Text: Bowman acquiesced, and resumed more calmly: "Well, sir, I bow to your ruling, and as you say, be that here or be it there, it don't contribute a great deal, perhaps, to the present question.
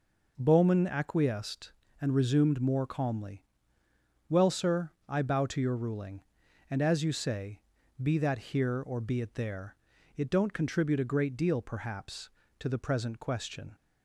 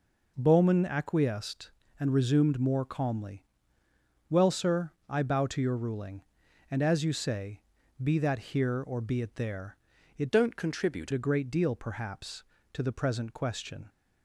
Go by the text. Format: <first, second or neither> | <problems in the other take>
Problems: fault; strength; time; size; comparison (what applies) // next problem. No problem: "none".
first | changes voice from "don't" to "contribute"; from 10.3 to 11.1 s; 0.8 s long